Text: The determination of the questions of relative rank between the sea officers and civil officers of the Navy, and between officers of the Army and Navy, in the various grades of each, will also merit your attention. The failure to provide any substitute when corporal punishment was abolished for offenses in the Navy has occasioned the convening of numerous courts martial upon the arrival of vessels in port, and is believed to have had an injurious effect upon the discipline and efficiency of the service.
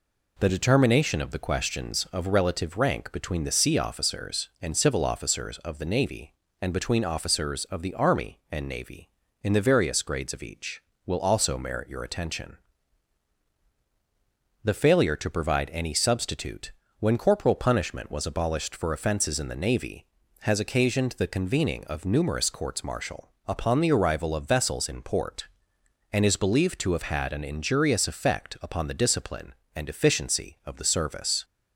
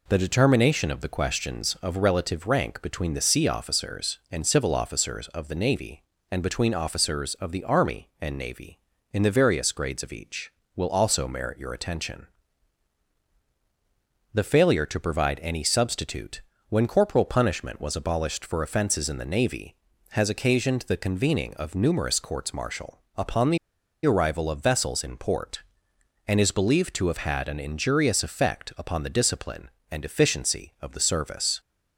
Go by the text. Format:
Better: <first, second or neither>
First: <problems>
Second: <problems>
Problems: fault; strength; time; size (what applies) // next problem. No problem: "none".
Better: first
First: pauses between "substitute" and "when"; slight; at 16.7 s; 0.28 s long // pauses between "martial" and "upon"; slight; at 23.3 s; 0.16 s long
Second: pauses between "substitute" and "when"; slight; at 16.4 s; 0.28 s long // pauses between "martial" and "upon"; slight; at 23.0 s; 0.16 s long // pauses between "the" and "arrival"; noticeable; at 23.5 s; 0.48 s long